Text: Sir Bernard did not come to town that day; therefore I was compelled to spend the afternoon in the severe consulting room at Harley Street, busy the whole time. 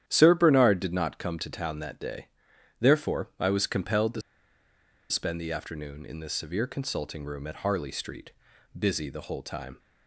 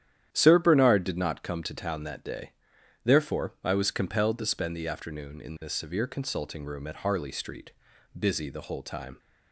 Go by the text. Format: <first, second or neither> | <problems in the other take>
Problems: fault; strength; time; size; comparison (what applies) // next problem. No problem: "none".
second | starts louder than the rest; strong; until 1.0 s; 10.5 dB; strong in the second // pauses between "to" and "spend"; noticeable; at 4.2 s; 0.89 s long